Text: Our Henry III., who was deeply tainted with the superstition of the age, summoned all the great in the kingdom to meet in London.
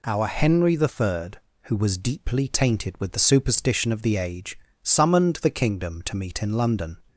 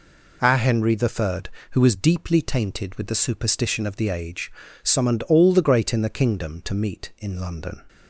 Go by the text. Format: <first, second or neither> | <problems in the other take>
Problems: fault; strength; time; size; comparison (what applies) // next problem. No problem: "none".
second | skips "all the great in"; at 5.3 s